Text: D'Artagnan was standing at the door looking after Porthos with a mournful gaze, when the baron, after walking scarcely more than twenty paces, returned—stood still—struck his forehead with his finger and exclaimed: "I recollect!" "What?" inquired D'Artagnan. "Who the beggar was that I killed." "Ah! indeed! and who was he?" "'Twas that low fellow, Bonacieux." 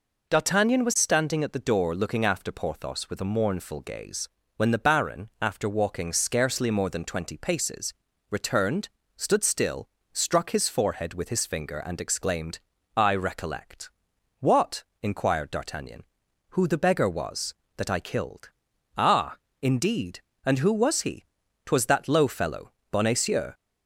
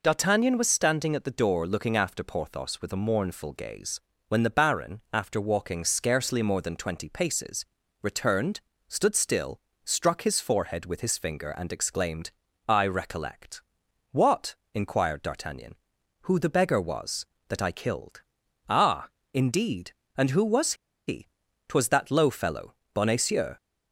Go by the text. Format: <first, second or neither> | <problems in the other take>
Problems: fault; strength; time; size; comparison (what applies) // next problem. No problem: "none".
first | pauses between "was" and "he"; slight; at 20.7 s; 0.32 s long